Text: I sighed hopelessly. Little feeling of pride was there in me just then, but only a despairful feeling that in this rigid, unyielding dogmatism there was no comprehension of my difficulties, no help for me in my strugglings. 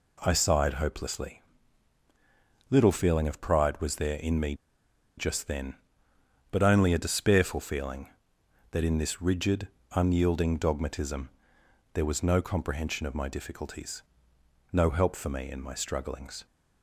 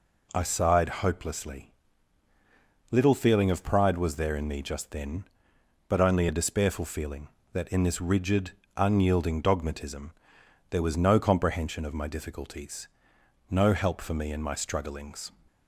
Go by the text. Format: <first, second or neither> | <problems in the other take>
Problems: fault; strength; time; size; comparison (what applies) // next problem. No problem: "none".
second | pauses between "me" and "just"; noticeable; at 4.5 s; 0.62 s long // pauses between "dogmatism" and "there"; noticeable; at 11.2 s; 0.64 s long; noticeable in the second